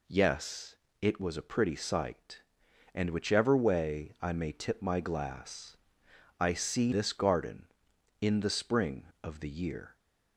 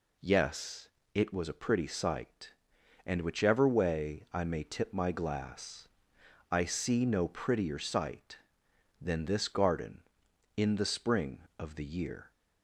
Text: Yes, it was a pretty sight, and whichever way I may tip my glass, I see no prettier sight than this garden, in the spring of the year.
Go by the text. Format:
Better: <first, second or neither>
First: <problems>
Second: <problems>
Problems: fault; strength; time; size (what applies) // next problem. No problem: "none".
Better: second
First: skips "no prettier sight than"; at 6.9 s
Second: none